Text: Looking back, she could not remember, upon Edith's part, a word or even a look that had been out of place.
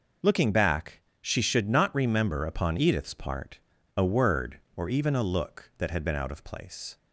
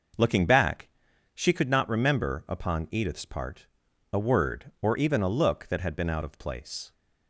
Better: second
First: says "should" for "could"; at 1.4 s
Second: none

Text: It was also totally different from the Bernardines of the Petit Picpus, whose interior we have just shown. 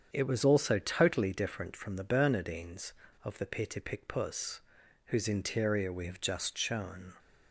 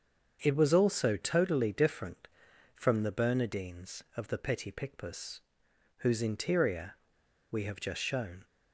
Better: first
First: starts louder than the rest; strong; until 1.1 s; 7.5 dB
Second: starts louder than the rest; until 1.4 s; 7 dB // pauses between "interior" and "we"; noticeable; at 6.9 s; 0.55 s long

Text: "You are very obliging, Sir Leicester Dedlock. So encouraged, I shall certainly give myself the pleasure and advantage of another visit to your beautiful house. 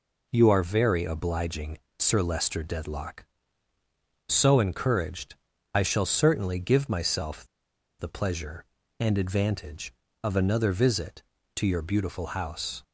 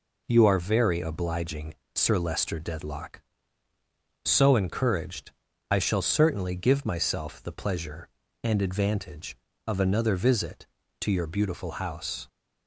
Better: second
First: pauses between "myself" and "the"; noticeable; at 7.4 s; 0.52 s long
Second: none

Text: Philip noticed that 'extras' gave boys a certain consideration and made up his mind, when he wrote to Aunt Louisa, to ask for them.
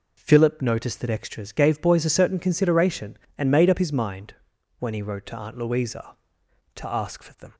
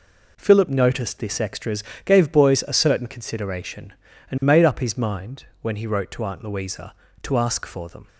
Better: first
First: none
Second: says "this" for "that"; at 1.1 s // pauses between "extras" and "gave"; slight; at 1.8 s; 0.22 s long

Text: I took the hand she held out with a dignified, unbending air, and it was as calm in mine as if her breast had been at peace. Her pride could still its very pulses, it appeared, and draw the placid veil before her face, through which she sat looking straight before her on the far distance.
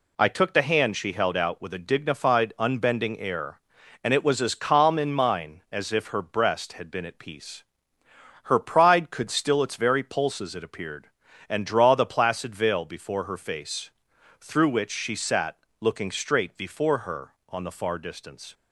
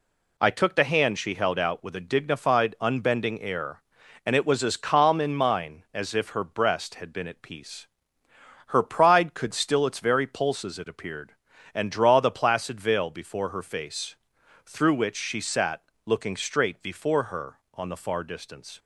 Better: neither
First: pauses between "sat" and "looking"; slight; at 15.5 s; 0.24 s long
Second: pauses between "sat" and "looking"; slight; at 15.8 s; 0.24 s long

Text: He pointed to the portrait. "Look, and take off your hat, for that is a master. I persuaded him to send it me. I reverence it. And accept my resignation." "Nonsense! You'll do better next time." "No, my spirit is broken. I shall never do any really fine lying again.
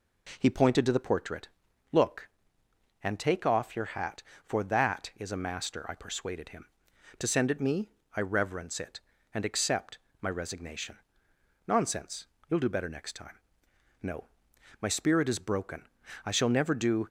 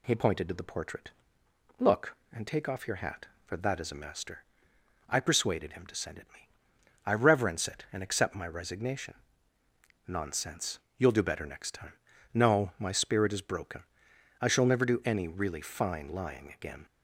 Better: second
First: pauses between "accept" and "my"; slight; at 9.9 s; 0.24 s long // stops before "any really fine lying again"; at 17.0 s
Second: none

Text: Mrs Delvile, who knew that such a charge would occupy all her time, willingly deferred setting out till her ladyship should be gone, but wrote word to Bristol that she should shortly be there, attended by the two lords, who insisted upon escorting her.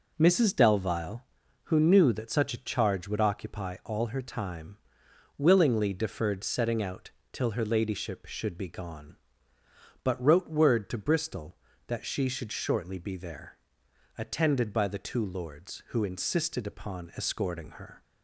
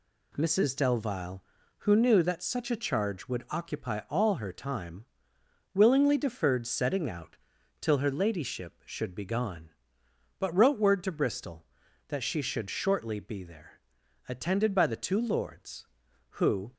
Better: first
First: pauses between "out" and "till"; slight; at 7.1 s; 0.22 s long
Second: pauses between "out" and "till"; noticeable; at 7.3 s; 0.46 s long // stops before "insisted upon escorting her"; at 16.7 s

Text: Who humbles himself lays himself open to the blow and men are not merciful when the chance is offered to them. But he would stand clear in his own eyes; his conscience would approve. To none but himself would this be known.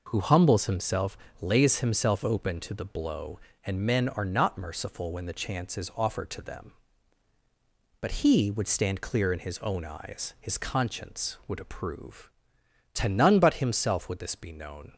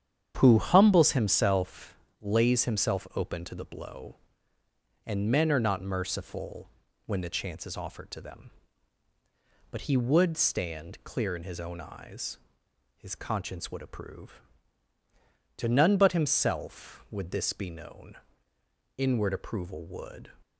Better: first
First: pauses between "himself" and "lays"; slight; at 1.1 s; 0.24 s long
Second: starts louder than the rest; strong; until 1.4 s; 8.5 dB // pauses between "himself" and "lays"; slight; at 1.9 s; 0.24 s long // pauses between "merciful" and "when"; at 6.6 s; 0.38 s long // goes on to say "Inward approval would"; from 18.9 s on; 1.3 s long

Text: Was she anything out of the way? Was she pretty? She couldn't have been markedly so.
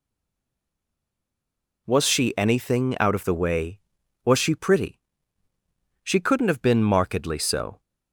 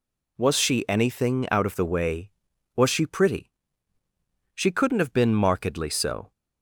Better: second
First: stays silent before the first word; noticeable; until 1.8 s; 1.8 s long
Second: none

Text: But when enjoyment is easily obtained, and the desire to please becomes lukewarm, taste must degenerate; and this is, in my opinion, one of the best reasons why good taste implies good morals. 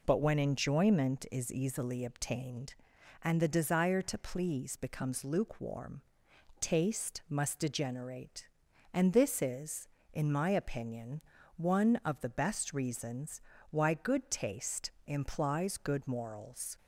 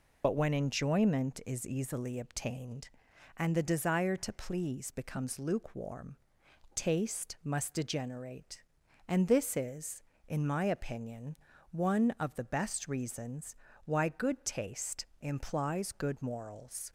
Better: first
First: pauses between "reasons" and "why"; slight; at 13.3 s; 0.30 s long // pauses between "taste" and "implies"; slight; at 14.8 s; 0.16 s long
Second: loses the start of "But"; at 0.2 s; 50 ms // pauses between "reasons" and "why"; slight; at 13.5 s; 0.30 s long // pauses between "taste" and "implies"; slight; at 15.0 s; 0.16 s long

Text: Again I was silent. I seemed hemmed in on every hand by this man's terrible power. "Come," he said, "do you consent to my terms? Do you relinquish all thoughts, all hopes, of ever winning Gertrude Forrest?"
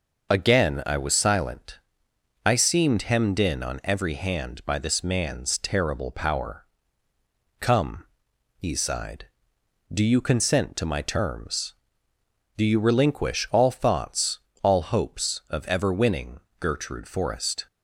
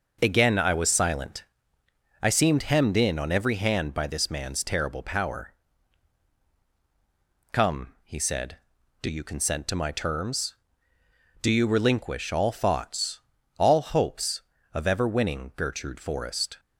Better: second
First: says "sighed" for "said"; at 8.7 s // pauses between "winning" and "Gertrude"; slight; at 16.4 s; 0.18 s long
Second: none

